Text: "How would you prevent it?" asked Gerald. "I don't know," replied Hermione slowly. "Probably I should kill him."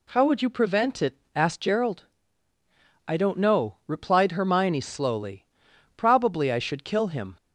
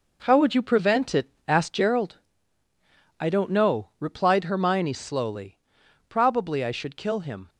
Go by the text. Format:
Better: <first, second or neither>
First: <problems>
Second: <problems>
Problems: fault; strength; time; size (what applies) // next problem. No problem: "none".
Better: first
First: none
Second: gets quieter; strong; throughout; 8 dB